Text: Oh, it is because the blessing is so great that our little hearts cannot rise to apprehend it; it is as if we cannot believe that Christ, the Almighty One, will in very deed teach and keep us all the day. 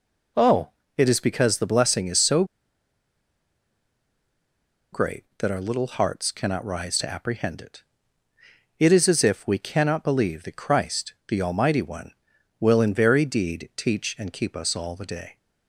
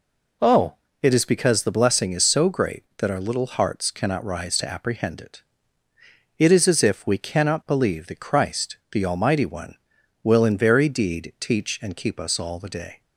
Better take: second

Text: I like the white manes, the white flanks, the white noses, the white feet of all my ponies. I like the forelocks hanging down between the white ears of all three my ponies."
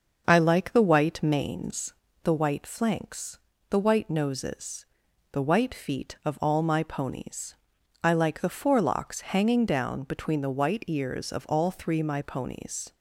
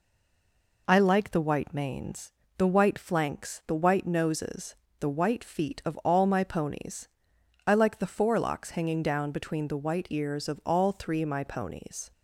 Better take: first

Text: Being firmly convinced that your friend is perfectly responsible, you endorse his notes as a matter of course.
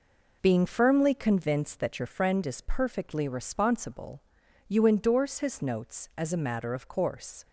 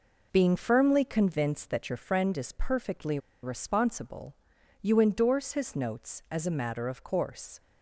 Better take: first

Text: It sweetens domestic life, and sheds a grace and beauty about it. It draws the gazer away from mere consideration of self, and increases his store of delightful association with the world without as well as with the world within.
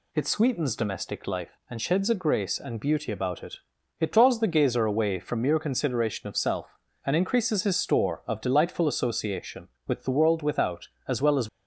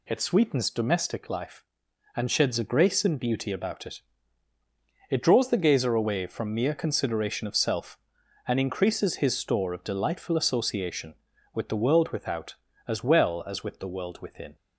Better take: second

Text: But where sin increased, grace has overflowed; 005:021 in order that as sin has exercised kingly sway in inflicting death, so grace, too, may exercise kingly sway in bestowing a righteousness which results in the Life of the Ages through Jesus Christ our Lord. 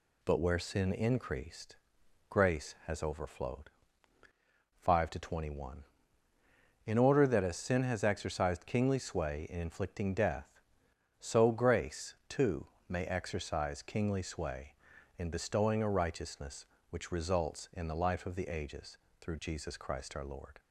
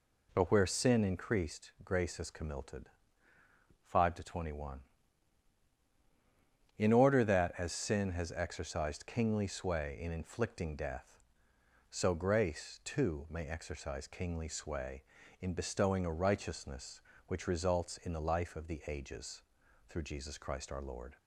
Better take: first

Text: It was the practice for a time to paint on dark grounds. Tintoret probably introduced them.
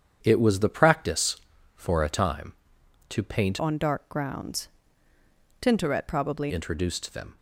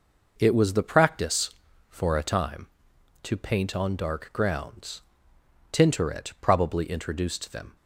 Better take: second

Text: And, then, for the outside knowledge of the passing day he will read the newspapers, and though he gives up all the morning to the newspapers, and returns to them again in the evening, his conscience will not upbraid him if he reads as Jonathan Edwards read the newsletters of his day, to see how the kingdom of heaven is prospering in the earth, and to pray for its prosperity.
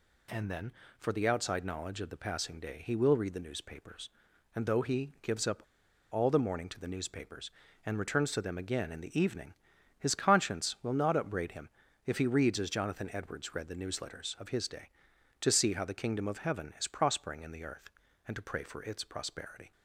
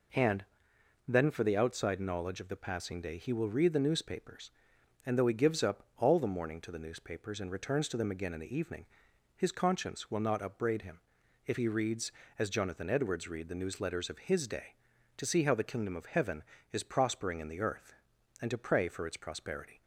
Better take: second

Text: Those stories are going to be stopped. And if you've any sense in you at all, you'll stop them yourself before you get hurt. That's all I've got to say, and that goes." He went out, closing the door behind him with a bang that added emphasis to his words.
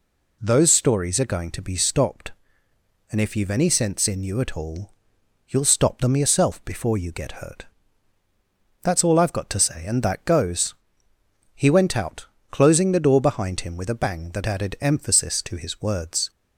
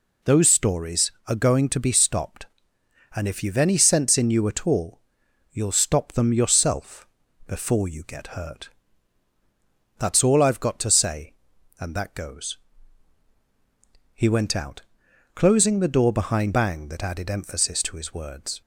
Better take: first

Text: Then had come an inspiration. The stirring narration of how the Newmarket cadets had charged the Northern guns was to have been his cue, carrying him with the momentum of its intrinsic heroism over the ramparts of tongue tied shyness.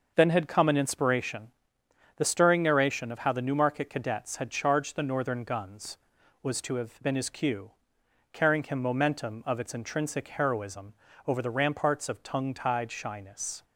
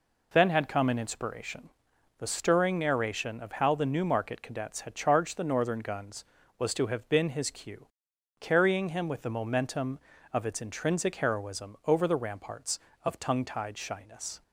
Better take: second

